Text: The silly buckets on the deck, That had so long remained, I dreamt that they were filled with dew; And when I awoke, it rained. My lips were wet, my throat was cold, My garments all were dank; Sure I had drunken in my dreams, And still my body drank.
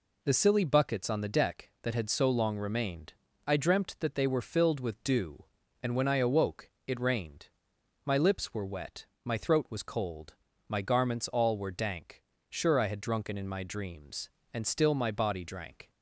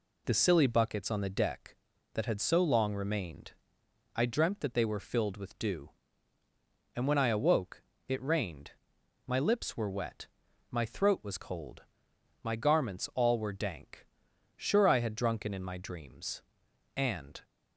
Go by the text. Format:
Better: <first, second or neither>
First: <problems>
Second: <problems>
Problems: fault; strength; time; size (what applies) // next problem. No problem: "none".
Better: first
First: none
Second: stops before "still my body drank"; at 17.4 s